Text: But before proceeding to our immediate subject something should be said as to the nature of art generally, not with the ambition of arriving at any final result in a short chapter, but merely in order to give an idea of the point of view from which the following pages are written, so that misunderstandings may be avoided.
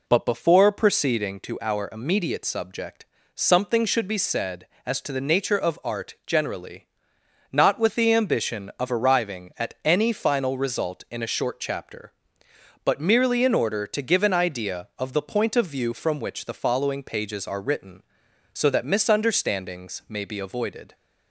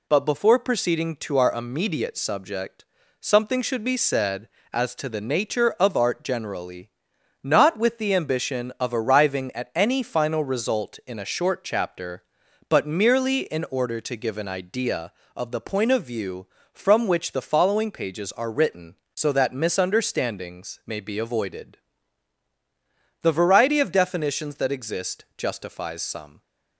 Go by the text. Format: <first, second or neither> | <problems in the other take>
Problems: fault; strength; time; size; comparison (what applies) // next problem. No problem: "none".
first | pauses between "subject" and "something"; slight; at 2.8 s; 0.36 s long; slight in the first // goes on to say "The variety of definitions that exist justifies some"; strong; from 23.2 s on; 3.1 s long